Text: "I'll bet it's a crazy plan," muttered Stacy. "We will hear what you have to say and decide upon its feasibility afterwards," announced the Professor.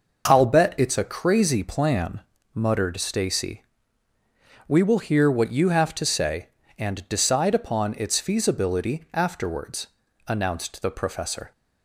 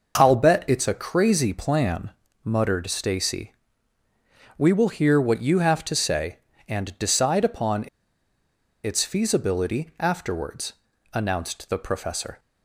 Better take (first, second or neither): first